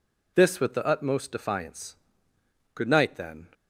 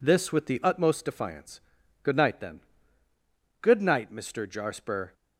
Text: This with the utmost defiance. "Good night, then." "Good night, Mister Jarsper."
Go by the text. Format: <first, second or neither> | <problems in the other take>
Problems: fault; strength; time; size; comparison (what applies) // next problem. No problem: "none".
second | stops before "Good night Mister Jarsper"; at 3.5 s